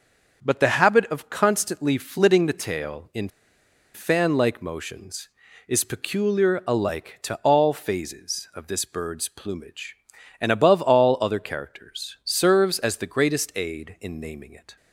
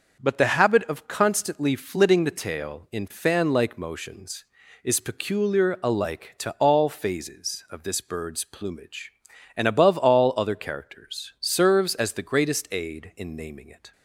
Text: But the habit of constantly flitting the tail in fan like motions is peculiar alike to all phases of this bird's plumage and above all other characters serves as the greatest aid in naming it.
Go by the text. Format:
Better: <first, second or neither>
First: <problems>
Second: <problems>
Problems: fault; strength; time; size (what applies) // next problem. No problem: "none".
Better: second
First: starts louder than the rest; noticeable; until 1.4 s; 6 dB // pauses between "in" and "fan"; noticeable; at 3.2 s; 0.66 s long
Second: starts louder than the rest; noticeable; until 1.2 s; 6 dB